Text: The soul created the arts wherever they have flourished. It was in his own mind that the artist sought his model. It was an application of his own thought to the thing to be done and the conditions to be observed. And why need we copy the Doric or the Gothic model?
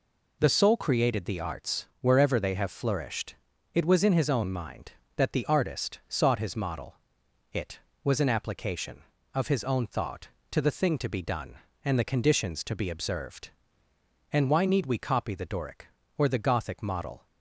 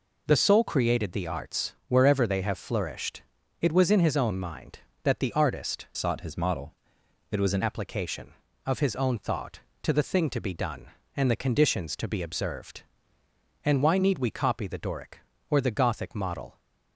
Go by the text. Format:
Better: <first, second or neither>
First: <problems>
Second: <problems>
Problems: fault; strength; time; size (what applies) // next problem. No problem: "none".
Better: first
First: none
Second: changes voice from "sought" to "an"; from 5.9 to 7.6 s; 1.7 s long